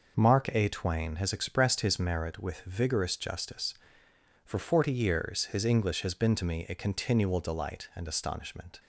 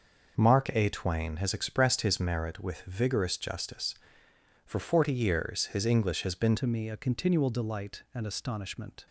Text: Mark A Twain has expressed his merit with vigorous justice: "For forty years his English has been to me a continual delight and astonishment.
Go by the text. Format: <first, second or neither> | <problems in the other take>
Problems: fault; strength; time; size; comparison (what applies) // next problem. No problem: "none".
first | changes voice at "to"; from 6.5 s on; 2.5 s long